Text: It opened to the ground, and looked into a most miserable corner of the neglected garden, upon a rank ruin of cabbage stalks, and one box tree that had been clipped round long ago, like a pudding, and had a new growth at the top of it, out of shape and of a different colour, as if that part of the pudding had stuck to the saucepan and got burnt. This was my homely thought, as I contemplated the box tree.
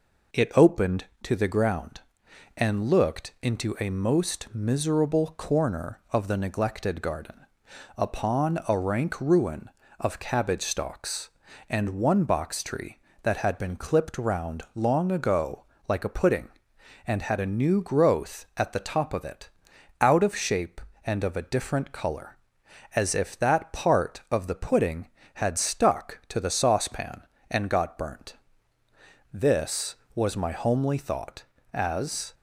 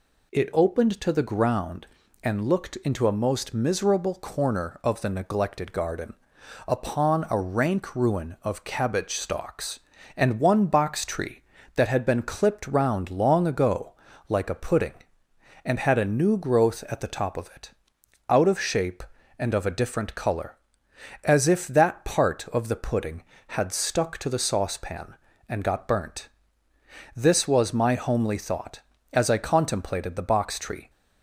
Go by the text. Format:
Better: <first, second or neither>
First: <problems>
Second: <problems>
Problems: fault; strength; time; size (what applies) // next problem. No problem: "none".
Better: second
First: stops before "I contemplated the box tree"; at 32.3 s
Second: none